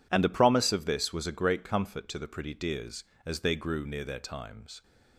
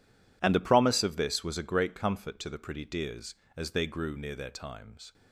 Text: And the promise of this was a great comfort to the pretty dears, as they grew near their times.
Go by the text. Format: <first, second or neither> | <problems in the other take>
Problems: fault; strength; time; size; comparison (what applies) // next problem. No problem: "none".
first | gets quieter; strong; throughout; 16 dB